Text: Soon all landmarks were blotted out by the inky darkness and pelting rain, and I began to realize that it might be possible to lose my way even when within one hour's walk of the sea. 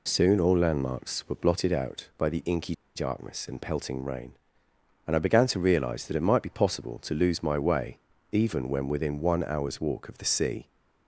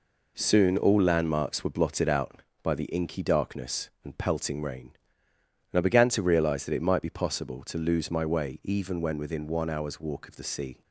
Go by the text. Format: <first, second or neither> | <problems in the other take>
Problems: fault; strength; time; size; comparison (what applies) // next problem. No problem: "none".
second | pauses between "inky" and "darkness"; slight; at 2.7 s; 0.20 s long // pauses between "way" and "even"; slight; at 7.9 s; 0.34 s long